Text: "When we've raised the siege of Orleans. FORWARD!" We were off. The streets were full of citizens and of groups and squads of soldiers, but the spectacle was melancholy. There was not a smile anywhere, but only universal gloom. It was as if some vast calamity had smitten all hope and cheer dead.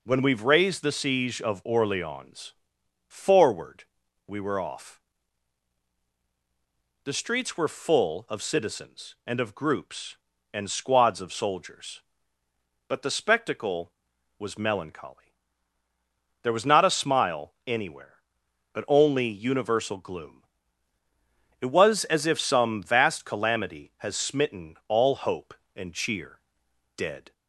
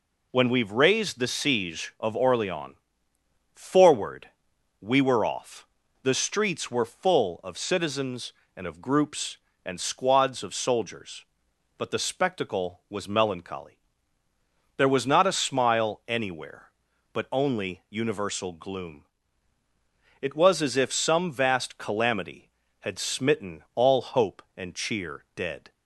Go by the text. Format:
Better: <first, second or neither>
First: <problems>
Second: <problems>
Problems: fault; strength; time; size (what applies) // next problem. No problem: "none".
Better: second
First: says "has" for "had"; at 23.9 s // pauses between "cheer" and "dead"; noticeable; at 26.4 s; 0.56 s long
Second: none